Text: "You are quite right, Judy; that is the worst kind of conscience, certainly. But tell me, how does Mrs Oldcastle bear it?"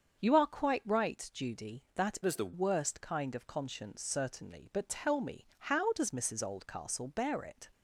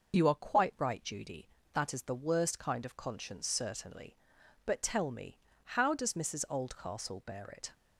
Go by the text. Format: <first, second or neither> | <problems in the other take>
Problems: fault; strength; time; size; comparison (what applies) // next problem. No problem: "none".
second | starts louder than the rest; until 1.2 s; 7 dB // changes voice from "is" to "the"; from 2.2 to 2.5 s; 0.3 s long